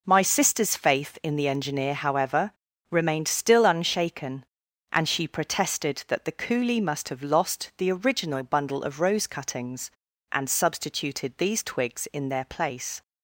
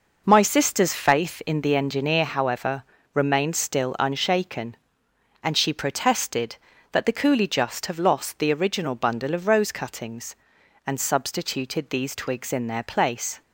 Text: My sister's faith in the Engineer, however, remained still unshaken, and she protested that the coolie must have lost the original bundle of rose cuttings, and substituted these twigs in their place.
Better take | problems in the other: first | says "just" for "must"; at 7.4 s

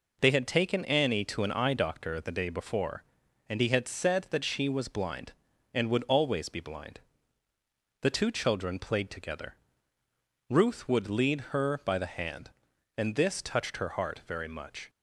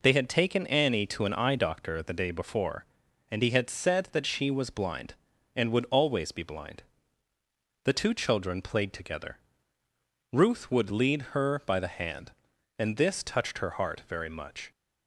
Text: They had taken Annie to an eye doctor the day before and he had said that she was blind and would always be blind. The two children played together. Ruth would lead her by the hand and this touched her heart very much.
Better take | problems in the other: neither | none

